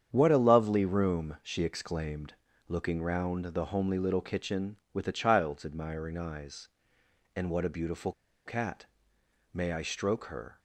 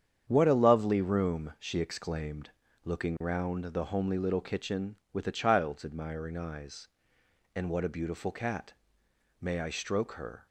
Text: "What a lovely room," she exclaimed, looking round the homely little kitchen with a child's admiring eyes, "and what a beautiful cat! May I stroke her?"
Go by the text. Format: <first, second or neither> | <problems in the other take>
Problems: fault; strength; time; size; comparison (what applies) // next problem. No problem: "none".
second | starts louder than the rest; strong; until 1.1 s; 8 dB; strong in the second // pauses between "beautiful" and "cat"; slight; at 8.1 s; 0.34 s long